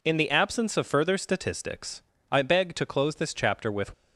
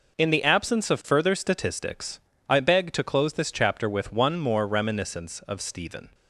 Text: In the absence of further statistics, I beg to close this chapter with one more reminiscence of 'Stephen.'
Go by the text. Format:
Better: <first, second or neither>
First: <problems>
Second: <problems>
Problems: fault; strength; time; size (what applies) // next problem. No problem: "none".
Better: second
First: stops before "one more reminiscence of Stephen"; at 3.9 s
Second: none